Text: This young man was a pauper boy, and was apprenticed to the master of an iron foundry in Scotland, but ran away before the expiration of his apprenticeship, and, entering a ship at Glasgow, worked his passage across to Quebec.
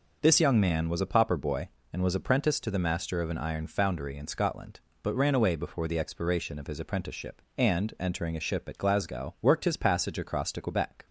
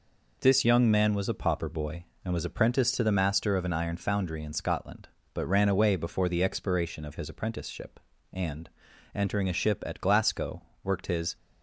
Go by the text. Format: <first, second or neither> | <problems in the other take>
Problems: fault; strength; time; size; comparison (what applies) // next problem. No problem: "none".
first | stops before "passage across to Quebec"; at 11.3 s